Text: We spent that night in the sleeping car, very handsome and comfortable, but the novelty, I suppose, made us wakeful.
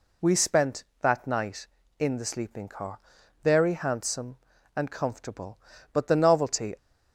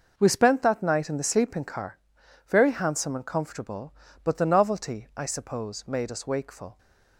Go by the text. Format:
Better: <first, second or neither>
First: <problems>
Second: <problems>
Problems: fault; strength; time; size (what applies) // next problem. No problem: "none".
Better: second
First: stops before "I suppose made us wakeful"; at 6.7 s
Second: none